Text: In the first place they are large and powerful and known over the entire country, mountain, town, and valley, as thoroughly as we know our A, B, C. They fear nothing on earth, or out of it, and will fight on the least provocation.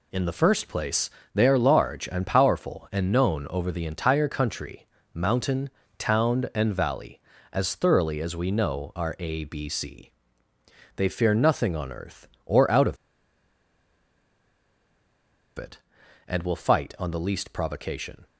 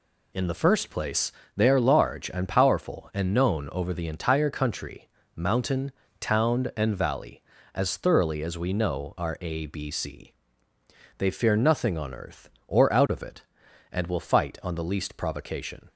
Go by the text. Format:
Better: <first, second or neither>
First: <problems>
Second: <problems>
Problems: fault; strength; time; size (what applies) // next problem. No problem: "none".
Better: second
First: pauses between "place" and "they"; slight; at 1.1 s; 0.24 s long // pauses between "of" and "it"; strong; at 12.9 s; 2.6 s long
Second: pauses between "place" and "they"; slight; at 1.3 s; 0.24 s long